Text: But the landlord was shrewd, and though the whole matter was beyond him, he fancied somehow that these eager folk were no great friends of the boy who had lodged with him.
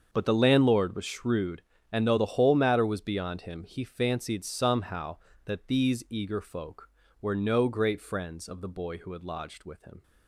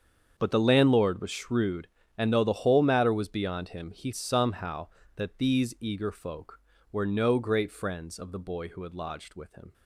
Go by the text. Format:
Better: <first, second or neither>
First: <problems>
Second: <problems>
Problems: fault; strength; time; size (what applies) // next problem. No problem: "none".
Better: first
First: starts louder than the rest; until 1.1 s; 7 dB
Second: starts louder than the rest; strong; until 1.3 s; 7 dB // skips "fancied"; at 4.1 s